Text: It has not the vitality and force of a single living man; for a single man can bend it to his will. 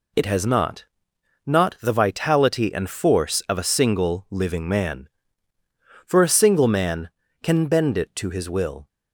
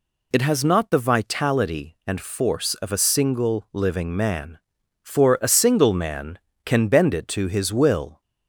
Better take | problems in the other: second | says "not" twice; at 1.4 s

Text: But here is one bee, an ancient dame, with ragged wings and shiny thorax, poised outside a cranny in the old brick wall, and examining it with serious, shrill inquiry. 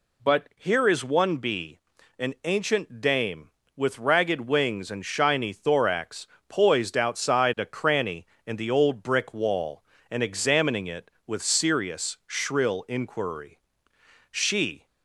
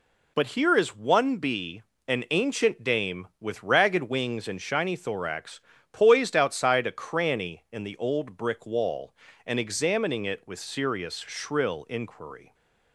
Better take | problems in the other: second | goes on to say "She"; from 14.3 s on; 0.54 s long

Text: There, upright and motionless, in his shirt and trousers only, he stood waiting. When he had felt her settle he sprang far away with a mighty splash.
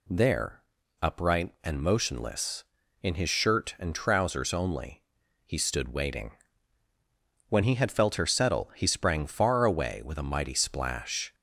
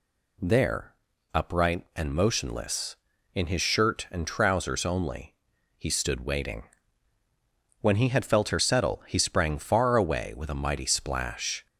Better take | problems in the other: neither | none

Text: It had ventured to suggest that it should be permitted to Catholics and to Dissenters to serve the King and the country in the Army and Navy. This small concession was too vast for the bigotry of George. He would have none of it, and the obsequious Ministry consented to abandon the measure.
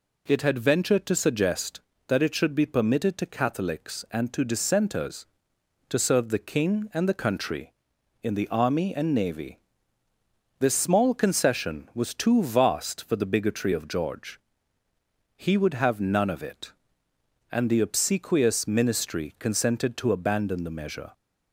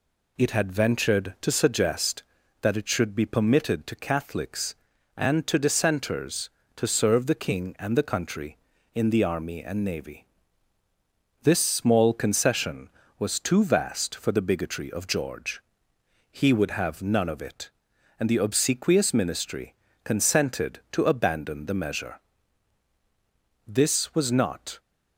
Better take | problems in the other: first | pauses between "Ministry" and "consented"; slight; at 19.7 s; 0.28 s long // goes on to say "This was not"; noticeable; from 23.6 s on; 1.1 s long

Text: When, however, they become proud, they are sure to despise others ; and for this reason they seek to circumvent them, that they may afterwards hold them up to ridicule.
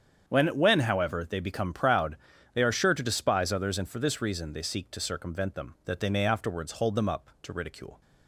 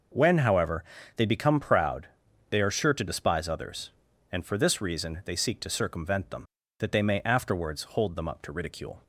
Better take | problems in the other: second | starts louder than the rest; strong; until 1.3 s; 8 dB // says "When" twice; at 0.5 s

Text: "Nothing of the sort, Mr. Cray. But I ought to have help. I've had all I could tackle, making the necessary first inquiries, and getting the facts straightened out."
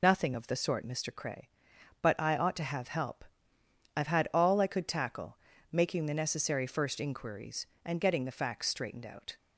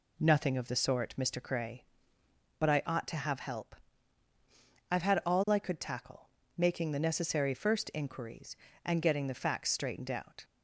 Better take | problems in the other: second | loses the start of "Nothing"; at 0.0 s; 55 ms

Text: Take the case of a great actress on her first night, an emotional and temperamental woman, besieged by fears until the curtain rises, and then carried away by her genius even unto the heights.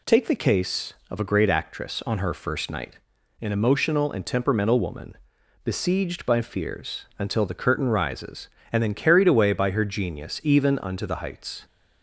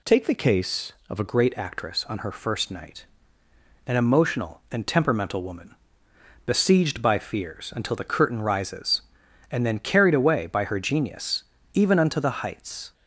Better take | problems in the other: first | changes voice at "great"; from 1.2 s on; 11.7 s long // pauses between "genius" and "even"; slight; at 11.4 s; 0.32 s long

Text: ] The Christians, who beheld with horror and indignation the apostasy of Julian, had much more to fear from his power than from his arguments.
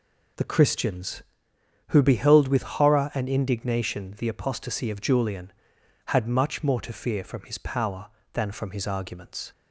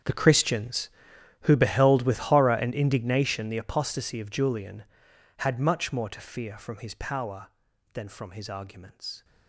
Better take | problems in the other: first | gets quieter; strong; throughout; 18.5 dB

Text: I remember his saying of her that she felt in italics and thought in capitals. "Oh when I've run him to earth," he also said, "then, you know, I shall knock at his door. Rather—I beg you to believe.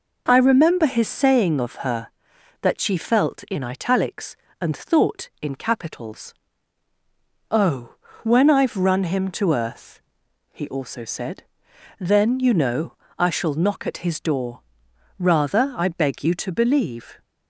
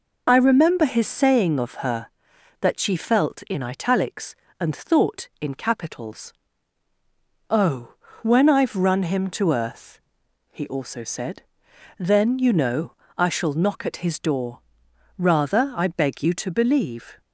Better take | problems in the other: first | loses the start of "I"; at 0.2 s; 25 ms // pauses between "Oh" and "when"; slight; at 7.9 s; 0.30 s long; slight in the first

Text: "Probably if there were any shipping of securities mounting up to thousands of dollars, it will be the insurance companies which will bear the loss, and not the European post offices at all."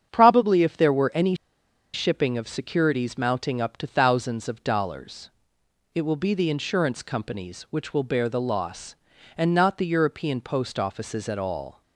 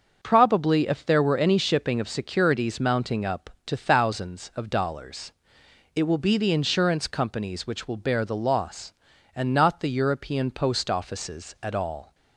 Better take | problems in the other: second | starts louder than the rest; strong; until 1.1 s; 8 dB; also in the second // pauses between "any" and "shipping"; noticeable; at 1.3 s; 0.59 s long

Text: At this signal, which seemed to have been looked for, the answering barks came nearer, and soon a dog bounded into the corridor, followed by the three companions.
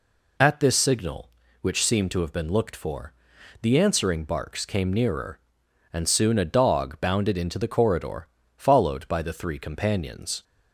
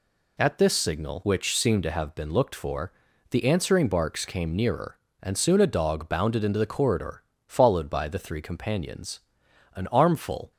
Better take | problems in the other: first | goes on to say "An armful"; noticeable; from 9.7 s on; 0.76 s long

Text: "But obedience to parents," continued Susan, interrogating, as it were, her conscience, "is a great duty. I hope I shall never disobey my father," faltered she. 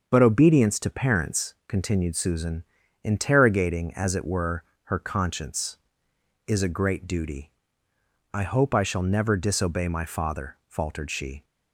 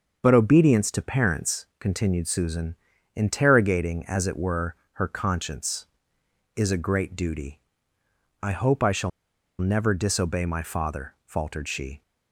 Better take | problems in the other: first | starts louder than the rest; until 1.2 s; 6.5 dB; also in the first // pauses between "shall" and "never"; noticeable; at 9.1 s; 0.51 s long

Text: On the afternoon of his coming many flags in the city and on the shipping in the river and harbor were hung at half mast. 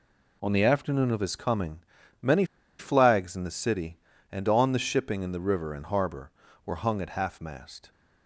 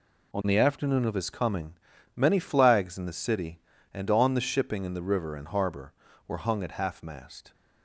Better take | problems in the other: second | pauses between "coming" and "many"; at 1.8 s; 0.40 s long; also in the second // pauses between "many" and "flags"; slight; at 2.4 s; 0.34 s long

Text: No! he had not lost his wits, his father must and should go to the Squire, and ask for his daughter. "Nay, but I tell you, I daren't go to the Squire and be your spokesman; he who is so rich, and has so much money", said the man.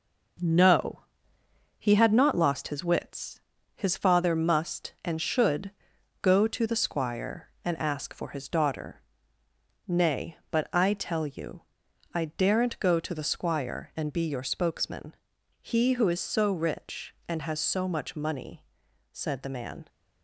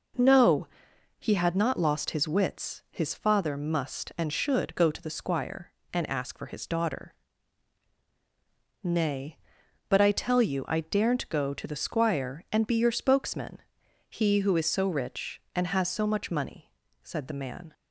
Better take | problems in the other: second | gets quieter; noticeable; throughout; 6 dB // pauses between "should" and "go"; noticeable; at 5.7 s; 0.50 s long

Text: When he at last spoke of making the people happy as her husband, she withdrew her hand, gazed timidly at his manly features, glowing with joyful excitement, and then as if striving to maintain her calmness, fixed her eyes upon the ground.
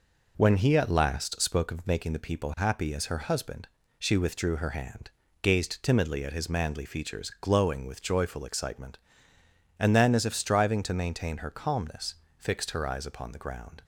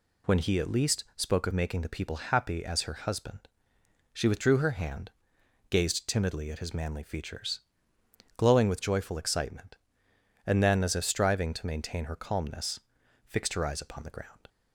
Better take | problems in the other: first | says "least" for "last"; at 0.7 s

